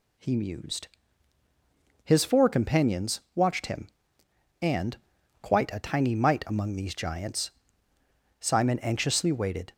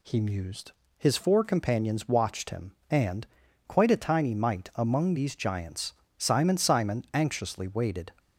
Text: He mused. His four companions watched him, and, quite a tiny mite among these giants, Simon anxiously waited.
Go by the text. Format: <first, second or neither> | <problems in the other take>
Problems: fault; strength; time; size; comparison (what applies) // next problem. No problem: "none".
first | says "Simon" twice; at 6.5 s